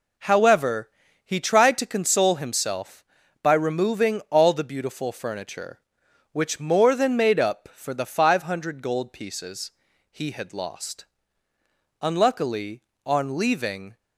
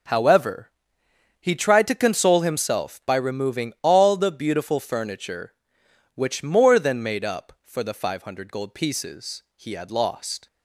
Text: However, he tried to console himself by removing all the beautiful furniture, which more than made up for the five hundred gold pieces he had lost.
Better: second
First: pauses between "pieces" and "he"; at 9.7 s; 0.40 s long // goes on to say "Unluckily on leaving"; strong; from 12.0 s on; 1.9 s long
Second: none

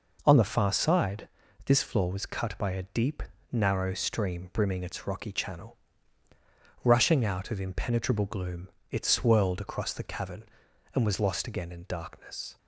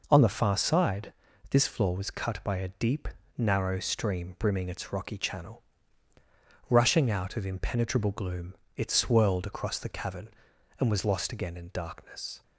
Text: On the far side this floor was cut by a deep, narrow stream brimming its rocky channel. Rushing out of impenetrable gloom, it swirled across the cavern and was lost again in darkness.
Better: neither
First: pauses between "side" and "this"; slight; at 1.2 s; 0.36 s long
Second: pauses between "side" and "this"; slight; at 1.1 s; 0.36 s long

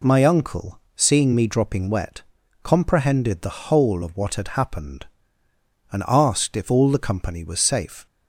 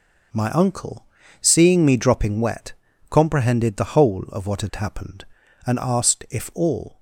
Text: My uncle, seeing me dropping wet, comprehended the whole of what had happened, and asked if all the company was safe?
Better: first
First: none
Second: stops before "the company was safe"; at 6.9 s

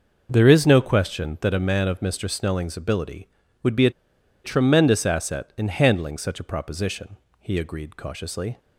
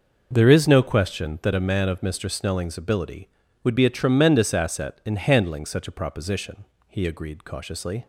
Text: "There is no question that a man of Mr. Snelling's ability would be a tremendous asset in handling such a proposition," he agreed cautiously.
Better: second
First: pauses between "a" and "tremendous"; noticeable; at 3.9 s; 0.53 s long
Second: none

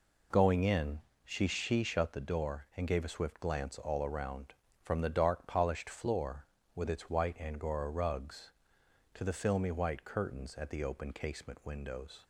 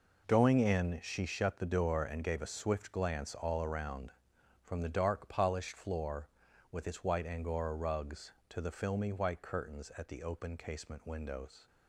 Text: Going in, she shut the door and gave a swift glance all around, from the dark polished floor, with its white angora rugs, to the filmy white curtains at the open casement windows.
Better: second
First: says "she" twice; at 1.4 s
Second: none

